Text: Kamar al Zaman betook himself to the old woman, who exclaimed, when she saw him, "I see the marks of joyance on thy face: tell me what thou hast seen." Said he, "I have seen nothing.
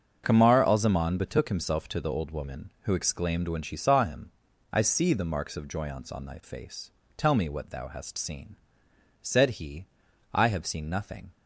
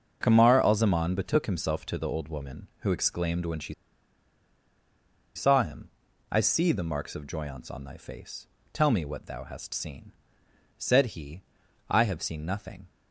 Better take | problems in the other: first | starts louder than the rest; until 1.2 s; 6.5 dB; also in the first // pauses between "she" and "saw"; strong; at 3.7 s; 1.6 s long

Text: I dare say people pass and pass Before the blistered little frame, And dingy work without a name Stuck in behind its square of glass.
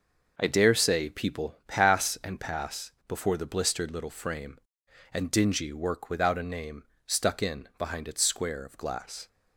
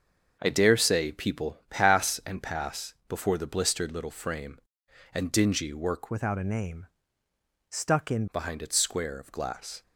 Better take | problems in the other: first | starts louder than the rest; until 1.4 s; 6.5 dB // pauses between "pass" and "Before"; slight; at 2.9 s; 0.16 s long; slight in the first // changes voice from "without" to "in"; from 6.0 to 8.2 s; 2.2 s long // pauses between "name" and "Stuck"; noticeable; at 6.8 s; 0.84 s long; slight in the first

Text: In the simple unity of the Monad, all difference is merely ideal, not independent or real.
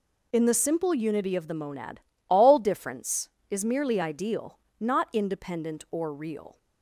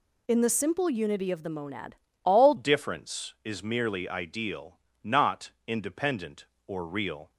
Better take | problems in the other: first | changes voice at "difference"; from 2.5 s on; 4.8 s long // pauses between "not" and "independent"; slight; at 5.4 s; 0.16 s long

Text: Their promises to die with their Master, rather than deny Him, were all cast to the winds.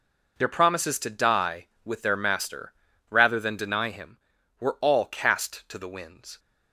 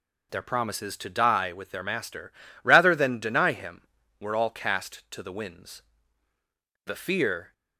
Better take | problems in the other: first | goes on to say "The fear"; noticeable; from 6.8 s on; 0.66 s long

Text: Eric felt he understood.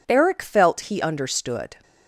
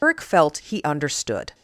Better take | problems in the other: first | loses the start of "Eric"; at 0.0 s; 155 ms

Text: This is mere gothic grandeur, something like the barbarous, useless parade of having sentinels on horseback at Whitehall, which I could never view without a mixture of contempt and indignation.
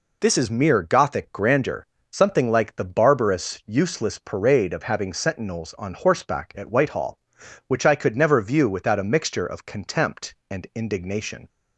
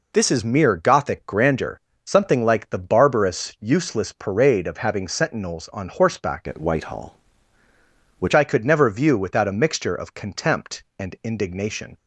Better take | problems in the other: first | changes voice from "at" to "which"; from 6.4 to 8.3 s; 1.9 s long

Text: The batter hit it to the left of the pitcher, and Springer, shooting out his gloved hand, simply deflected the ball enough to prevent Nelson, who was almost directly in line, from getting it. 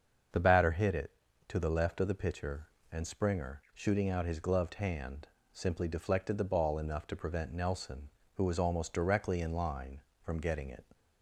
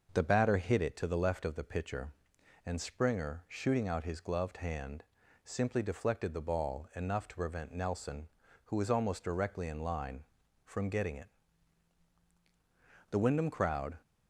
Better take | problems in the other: first | starts louder than the rest; until 1.1 s; 6 dB; also in the first // goes on to say "The Wyndham crowd"; noticeable; from 13.1 s on; 0.88 s long

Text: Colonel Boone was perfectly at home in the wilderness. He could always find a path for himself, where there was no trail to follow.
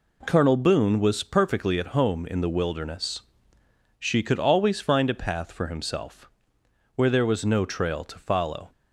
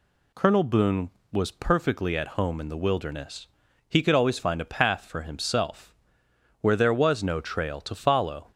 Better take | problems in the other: second | says "She" for "He"; at 3.9 s

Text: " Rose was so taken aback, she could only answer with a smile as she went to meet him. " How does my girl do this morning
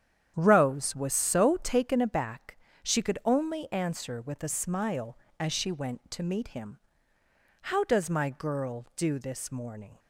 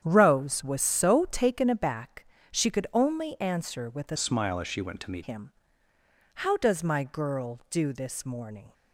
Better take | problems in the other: first | starts louder than the rest; strong; until 1.0 s; 9 dB; strong in the first // changes voice from "smile" to "meet"; from 4.1 to 5.2 s; 1.1 s long

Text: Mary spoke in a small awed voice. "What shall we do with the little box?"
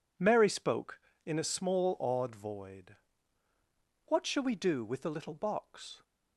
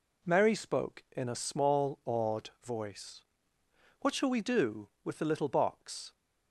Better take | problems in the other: second | says "void" for "voice"; at 2.3 s

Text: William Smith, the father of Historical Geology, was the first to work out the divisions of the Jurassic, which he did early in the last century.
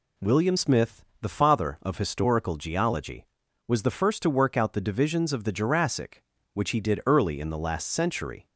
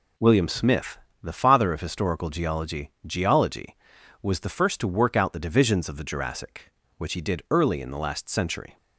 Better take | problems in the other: first | says "Geology" twice; at 3.0 s

